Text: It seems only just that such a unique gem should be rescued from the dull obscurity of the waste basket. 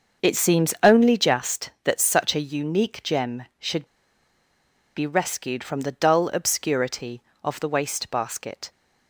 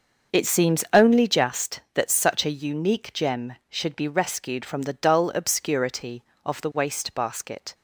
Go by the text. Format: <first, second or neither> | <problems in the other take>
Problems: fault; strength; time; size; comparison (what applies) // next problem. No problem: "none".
second | starts louder than the rest; until 1.3 s; 6.5 dB; also in the second // pauses between "should" and "be"; at 3.8 s; 1.1 s long